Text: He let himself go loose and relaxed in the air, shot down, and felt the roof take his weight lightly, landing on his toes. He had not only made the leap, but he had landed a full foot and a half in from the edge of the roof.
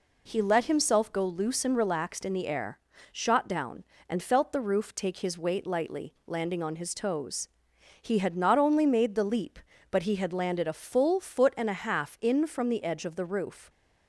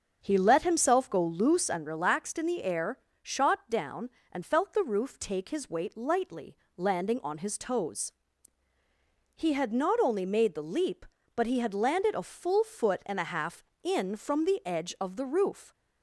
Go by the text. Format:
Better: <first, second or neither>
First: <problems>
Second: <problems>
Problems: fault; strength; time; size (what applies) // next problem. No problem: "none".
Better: first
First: none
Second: starts louder than the rest; until 1.5 s; 6.5 dB